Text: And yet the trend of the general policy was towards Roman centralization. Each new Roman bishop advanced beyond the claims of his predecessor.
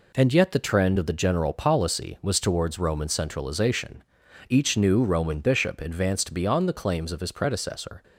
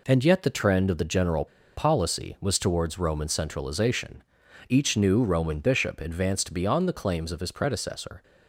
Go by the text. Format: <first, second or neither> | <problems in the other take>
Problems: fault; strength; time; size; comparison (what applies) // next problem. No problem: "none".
first | pauses between "general" and "policy"; slight; at 1.4 s; 0.30 s long